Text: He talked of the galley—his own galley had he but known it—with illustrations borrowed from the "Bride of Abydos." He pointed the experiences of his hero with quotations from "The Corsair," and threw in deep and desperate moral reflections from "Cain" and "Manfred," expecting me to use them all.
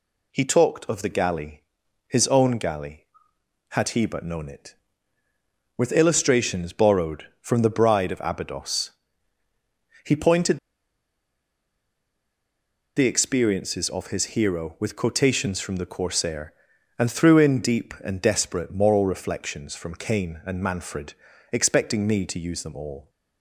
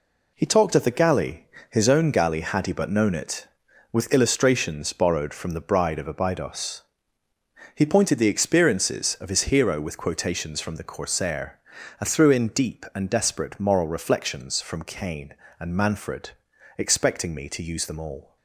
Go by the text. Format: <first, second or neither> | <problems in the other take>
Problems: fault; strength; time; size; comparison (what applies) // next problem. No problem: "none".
second | pauses between "pointed" and "the"; strong; at 10.5 s; 2.3 s long